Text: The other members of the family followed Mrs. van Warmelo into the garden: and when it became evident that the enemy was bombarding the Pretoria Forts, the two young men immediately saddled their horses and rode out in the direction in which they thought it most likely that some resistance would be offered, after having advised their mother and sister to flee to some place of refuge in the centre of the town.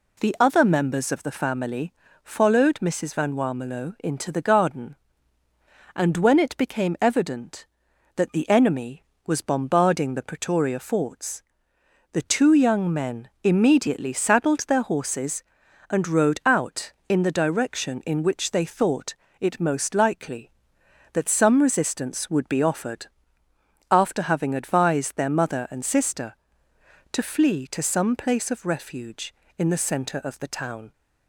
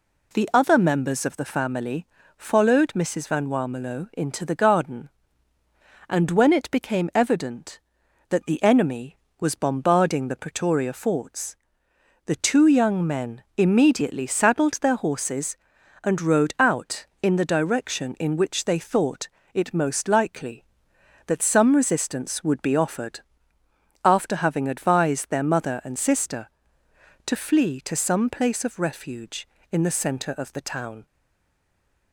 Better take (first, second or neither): first